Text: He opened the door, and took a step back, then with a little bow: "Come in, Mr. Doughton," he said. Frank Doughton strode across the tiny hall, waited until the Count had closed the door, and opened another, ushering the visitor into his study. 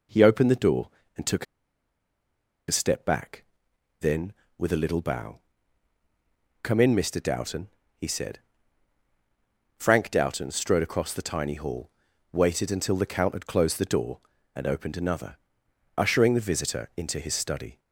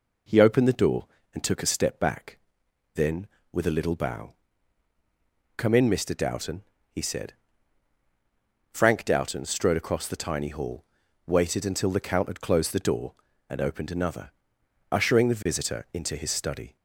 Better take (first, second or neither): second